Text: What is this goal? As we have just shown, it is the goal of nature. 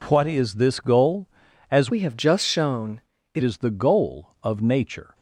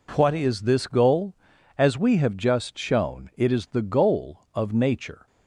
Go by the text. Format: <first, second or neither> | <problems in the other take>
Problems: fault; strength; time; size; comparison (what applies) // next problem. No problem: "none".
second | changes voice from "we" to "it"; from 1.8 to 3.4 s; 1.6 s long